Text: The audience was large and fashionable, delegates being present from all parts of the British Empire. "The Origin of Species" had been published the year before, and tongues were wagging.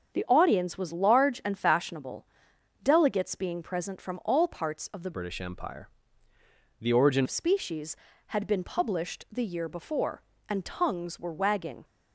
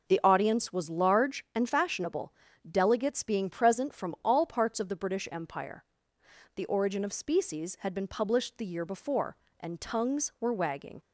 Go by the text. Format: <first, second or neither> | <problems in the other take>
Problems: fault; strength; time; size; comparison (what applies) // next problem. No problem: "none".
second | starts louder than the rest; until 1.1 s; 7 dB // changes voice from "British" to "Origin"; from 5.1 to 7.2 s; 2.1 s long